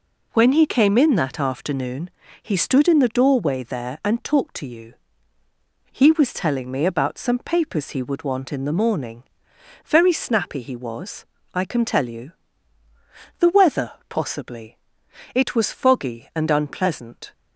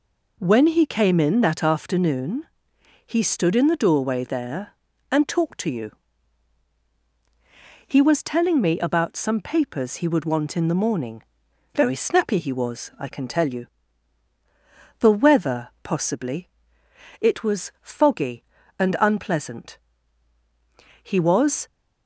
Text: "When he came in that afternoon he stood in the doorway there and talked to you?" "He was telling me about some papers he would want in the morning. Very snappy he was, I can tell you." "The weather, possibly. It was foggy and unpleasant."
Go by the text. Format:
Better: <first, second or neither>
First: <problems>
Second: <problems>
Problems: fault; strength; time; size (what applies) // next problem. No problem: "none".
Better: first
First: pauses between "afternoon" and "he"; slight; at 2.0 s; 0.32 s long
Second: pauses between "afternoon" and "he"; noticeable; at 2.4 s; 0.58 s long // goes on to say "He was"; noticeable; from 21.0 s on; 0.64 s long